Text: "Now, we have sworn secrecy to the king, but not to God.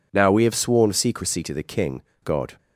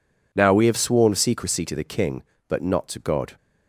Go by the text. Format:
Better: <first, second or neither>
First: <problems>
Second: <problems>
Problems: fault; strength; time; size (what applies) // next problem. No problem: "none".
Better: second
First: skips "but not to"; at 2.1 s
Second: none